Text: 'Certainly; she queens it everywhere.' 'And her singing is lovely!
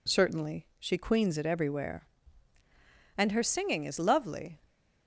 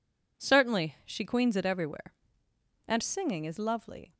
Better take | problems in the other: first | skips "her"; at 3.0 s

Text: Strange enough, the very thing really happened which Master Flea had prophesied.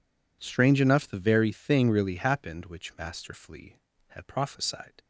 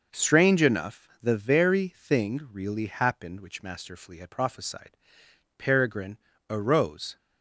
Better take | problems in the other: first | goes on to say "Peregrine arose"; from 5.5 s on; 1.6 s long

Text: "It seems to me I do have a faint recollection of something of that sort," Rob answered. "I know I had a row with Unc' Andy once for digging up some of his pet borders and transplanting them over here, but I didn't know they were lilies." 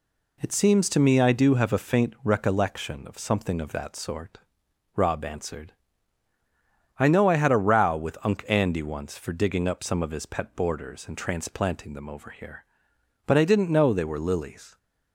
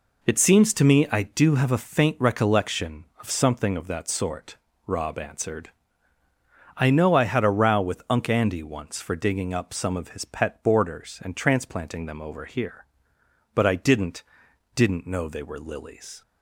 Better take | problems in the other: first | says "didn't" twice; at 14.7 s

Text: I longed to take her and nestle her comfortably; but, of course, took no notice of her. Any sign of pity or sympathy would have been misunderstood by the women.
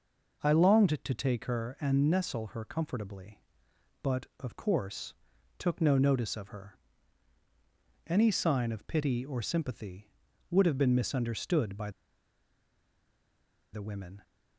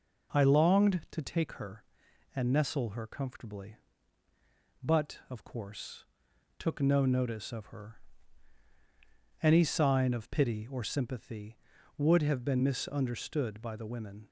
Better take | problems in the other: second | pauses between "by" and "the"; strong; at 11.8 s; 1.8 s long

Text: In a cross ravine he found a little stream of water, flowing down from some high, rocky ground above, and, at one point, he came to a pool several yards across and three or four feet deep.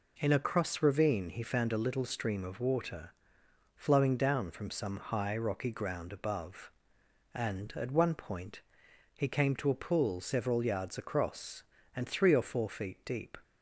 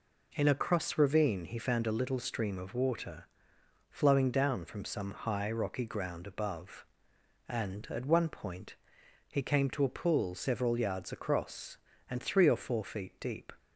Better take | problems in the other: neither | none

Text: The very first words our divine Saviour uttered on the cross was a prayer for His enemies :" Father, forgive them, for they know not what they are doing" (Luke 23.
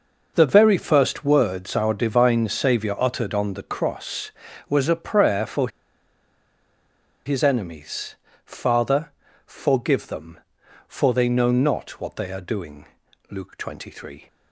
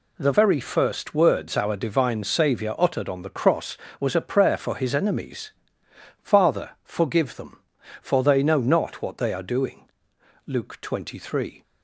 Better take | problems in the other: second | pauses between "for" and "His"; strong; at 5.6 s; 1.5 s long

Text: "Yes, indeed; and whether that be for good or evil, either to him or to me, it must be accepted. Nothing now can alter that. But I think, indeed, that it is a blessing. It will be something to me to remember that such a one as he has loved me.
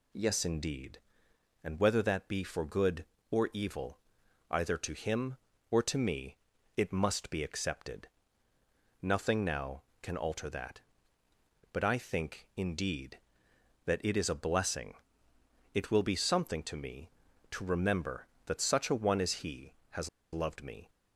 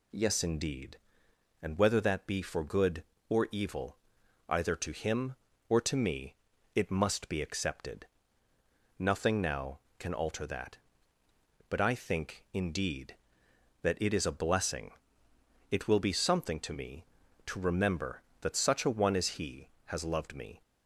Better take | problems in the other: second | pauses between "has" and "loved"; slight; at 20.0 s; 0.25 s long

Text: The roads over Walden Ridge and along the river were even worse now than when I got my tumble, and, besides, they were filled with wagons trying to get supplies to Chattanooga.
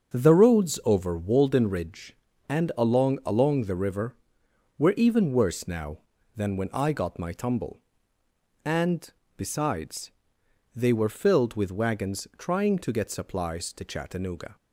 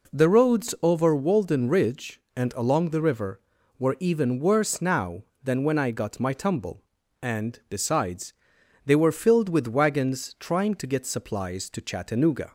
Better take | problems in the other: second | starts louder than the rest; until 1.2 s; 6.5 dB // says "along" twice; at 3.2 s

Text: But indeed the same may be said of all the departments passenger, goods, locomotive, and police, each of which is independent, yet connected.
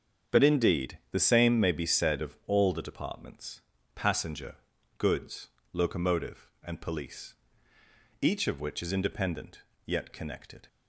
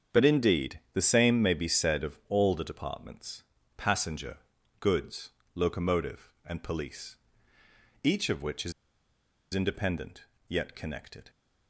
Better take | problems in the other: first | starts louder than the rest; strong; until 1.2 s; 7.5 dB; strong in the first // pauses between "departments" and "passenger"; slight; at 3.4 s; 0.34 s long; slight in the first // pauses between "is" and "independent"; noticeable; at 8.7 s; 0.81 s long

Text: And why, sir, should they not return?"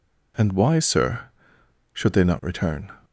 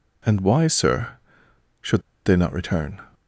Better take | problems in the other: first | pauses between "should" and "they"; slight; at 2.0 s; 0.24 s long

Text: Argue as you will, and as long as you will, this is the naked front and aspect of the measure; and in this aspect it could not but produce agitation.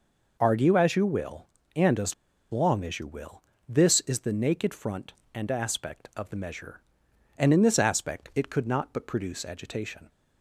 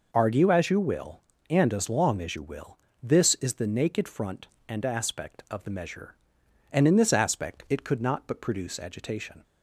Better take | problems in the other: second | pauses between "as" and "long"; at 2.1 s; 0.37 s long

